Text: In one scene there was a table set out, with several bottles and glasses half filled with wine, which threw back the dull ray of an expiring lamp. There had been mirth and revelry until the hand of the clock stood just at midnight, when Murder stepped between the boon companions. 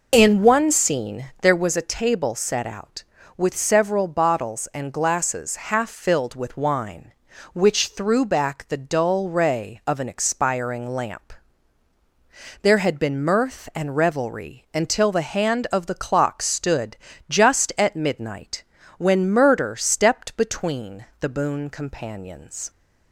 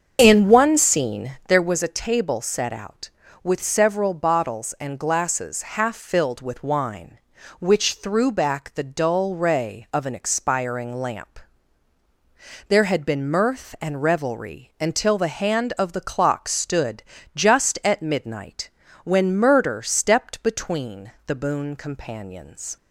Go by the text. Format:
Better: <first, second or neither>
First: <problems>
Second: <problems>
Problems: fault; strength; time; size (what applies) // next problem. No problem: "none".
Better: first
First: pauses between "stood" and "just"; slight; at 16.9 s; 0.32 s long // pauses between "between" and "the"; slight; at 21.0 s; 0.16 s long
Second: starts louder than the rest; until 1.4 s; 7 dB // pauses between "stood" and "just"; slight; at 17.0 s; 0.32 s long // pauses between "between" and "the"; slight; at 21.1 s; 0.16 s long